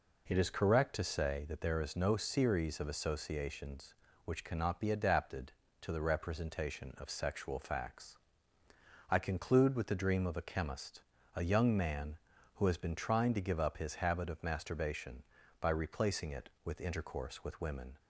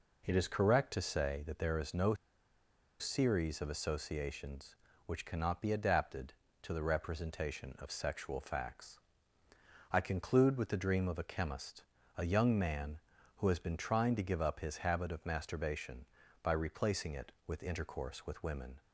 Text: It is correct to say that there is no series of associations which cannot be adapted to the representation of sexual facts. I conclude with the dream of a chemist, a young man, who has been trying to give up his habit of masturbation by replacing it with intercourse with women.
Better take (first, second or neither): first